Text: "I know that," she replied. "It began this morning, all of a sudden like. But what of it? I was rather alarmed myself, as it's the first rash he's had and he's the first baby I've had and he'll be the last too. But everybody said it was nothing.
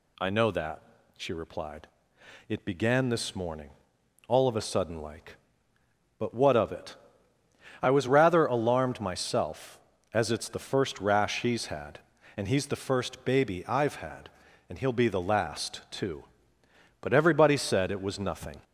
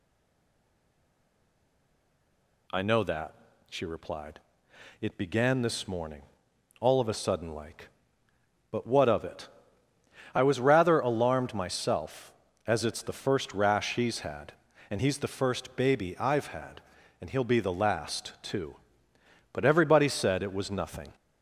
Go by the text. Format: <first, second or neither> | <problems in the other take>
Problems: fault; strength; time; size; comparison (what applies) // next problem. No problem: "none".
first | stays silent before the first word; strong; until 2.6 s; 2.6 s long